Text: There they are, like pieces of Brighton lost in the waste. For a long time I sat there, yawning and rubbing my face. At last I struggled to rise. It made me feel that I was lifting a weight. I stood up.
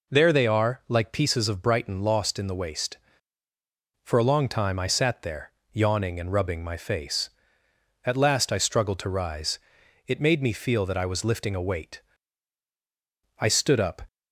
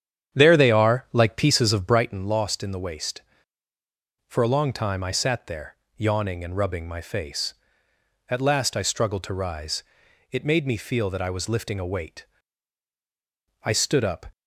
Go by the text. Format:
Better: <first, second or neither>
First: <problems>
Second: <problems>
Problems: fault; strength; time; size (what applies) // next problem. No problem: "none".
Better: first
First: none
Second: starts louder than the rest; strong; until 2.1 s; 9 dB